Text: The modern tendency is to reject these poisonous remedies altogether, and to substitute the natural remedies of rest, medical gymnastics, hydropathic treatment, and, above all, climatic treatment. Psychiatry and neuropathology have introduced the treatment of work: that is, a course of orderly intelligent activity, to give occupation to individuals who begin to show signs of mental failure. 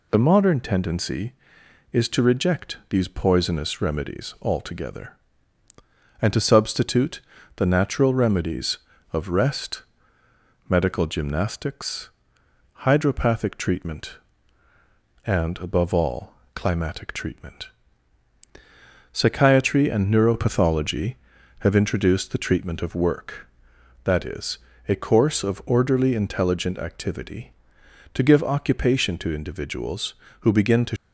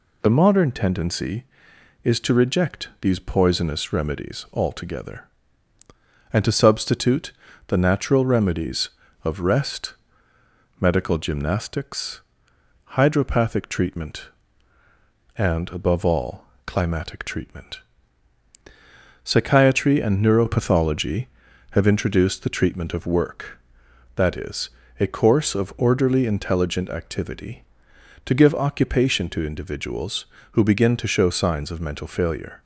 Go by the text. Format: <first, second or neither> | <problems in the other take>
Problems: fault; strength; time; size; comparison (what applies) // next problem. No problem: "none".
second | pauses between "substitute" and "the"; slight; at 7.1 s; 0.36 s long; slight in the second // stops before "show signs of mental failure"; at 30.9 s